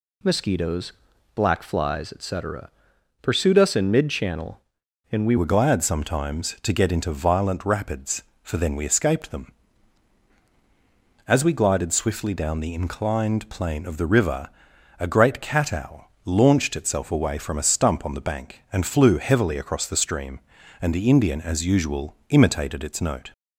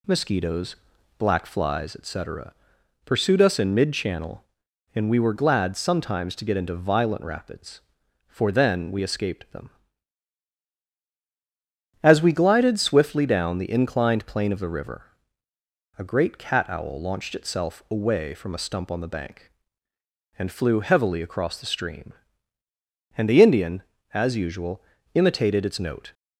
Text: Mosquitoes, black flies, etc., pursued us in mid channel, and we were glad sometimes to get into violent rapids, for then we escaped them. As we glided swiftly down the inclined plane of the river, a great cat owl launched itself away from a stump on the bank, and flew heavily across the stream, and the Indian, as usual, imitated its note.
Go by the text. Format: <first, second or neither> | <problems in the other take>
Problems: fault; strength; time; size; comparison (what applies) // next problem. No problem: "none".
second | changes voice at "were"; from 5.3 s on; 18.0 s long // pauses between "owl" and "launched"; slight; at 16.0 s; 0.16 s long